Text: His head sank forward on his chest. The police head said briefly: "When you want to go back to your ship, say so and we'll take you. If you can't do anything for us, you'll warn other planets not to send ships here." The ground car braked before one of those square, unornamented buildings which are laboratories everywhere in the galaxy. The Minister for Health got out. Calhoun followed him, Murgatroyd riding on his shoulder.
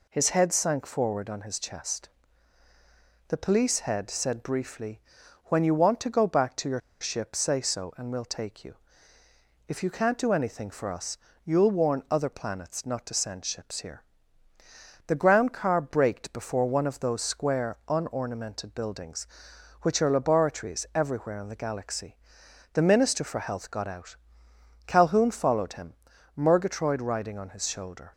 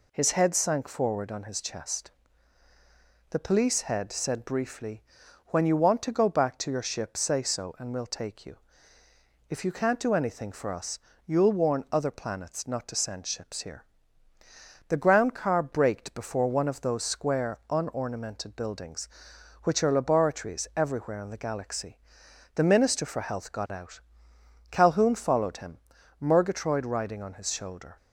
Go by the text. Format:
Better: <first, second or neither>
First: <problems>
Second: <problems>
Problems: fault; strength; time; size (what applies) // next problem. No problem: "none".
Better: second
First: pauses between "your" and "ship"; slight; at 6.7 s; 0.21 s long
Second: none